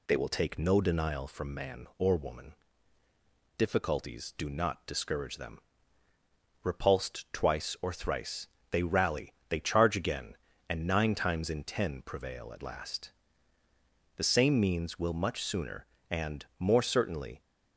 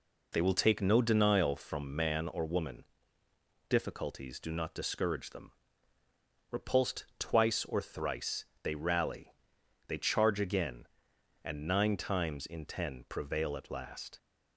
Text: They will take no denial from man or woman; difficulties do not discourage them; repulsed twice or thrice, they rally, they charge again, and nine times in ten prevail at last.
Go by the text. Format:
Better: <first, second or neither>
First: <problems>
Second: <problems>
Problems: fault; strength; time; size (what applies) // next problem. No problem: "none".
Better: second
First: goes on to say "The same means will much sooner and more certainly"; strong; from 14.1 s on; 3.2 s long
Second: none